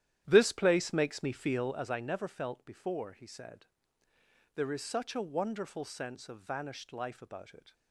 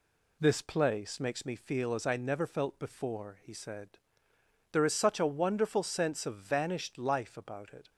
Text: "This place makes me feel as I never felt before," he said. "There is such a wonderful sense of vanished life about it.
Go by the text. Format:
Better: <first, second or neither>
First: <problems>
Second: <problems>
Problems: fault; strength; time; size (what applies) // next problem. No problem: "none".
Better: second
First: starts louder than the rest; strong; until 1.9 s; 11.5 dB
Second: none